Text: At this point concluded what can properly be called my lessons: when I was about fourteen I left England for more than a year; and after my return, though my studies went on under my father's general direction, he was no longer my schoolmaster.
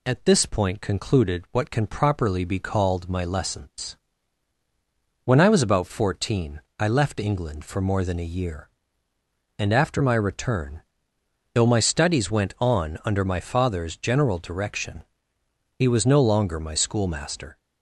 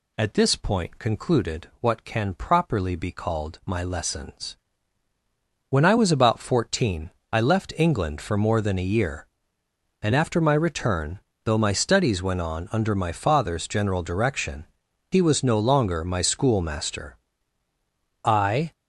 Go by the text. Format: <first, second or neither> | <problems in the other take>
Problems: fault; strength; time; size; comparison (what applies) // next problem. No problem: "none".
first | pauses between "fourteen" and "I"; slight; at 7.0 s; 0.22 s long; slight in the first // goes on to say "I"; from 18.2 s on; 0.50 s long